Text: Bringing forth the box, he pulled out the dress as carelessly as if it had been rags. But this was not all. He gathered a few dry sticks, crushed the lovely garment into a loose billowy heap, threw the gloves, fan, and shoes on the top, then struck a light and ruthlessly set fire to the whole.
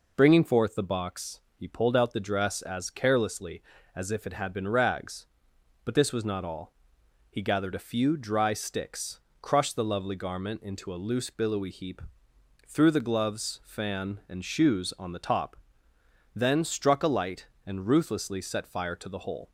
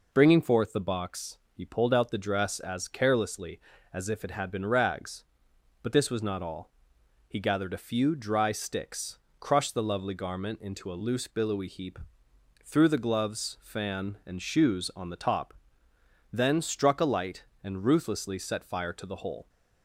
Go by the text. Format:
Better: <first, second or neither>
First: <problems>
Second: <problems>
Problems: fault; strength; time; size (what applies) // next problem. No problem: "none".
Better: neither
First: none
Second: none